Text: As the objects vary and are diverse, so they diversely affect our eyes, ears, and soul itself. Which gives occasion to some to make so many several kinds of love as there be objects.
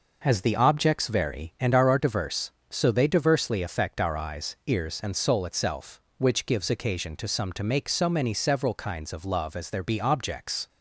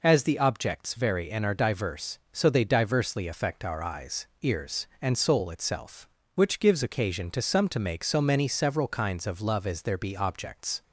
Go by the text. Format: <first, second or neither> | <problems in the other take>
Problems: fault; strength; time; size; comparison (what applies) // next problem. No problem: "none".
second | says "are" twice; at 1.8 s